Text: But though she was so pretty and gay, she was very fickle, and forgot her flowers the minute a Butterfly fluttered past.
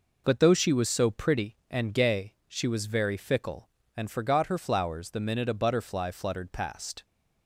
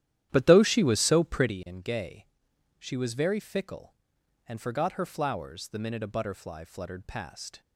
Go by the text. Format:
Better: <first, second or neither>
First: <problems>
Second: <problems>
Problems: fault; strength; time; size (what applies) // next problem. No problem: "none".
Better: first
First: none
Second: starts louder than the rest; strong; until 1.5 s; 12 dB